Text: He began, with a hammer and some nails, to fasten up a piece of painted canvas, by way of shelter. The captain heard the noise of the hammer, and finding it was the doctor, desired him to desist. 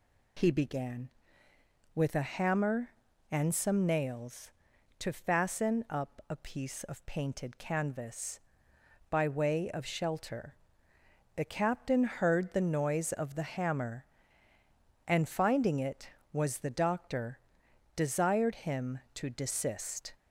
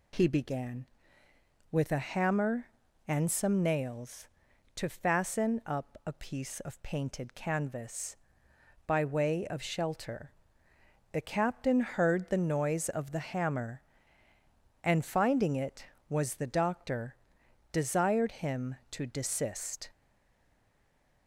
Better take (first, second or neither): first